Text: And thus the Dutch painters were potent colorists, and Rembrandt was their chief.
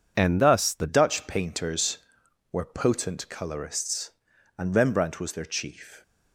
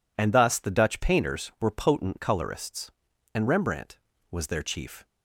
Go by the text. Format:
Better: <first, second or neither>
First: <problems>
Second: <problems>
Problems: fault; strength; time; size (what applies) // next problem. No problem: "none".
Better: second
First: changes voice at "Dutch"; from 0.8 s on; 5.2 s long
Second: none